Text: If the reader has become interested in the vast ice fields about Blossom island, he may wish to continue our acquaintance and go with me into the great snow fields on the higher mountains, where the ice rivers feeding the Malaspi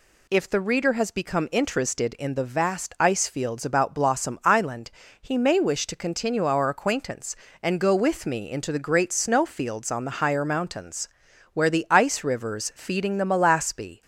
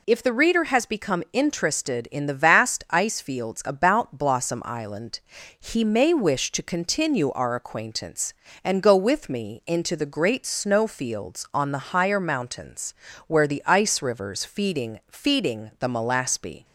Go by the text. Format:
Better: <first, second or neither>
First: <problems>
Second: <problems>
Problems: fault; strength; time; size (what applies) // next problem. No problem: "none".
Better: first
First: none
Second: says "feeding" twice; at 15.1 s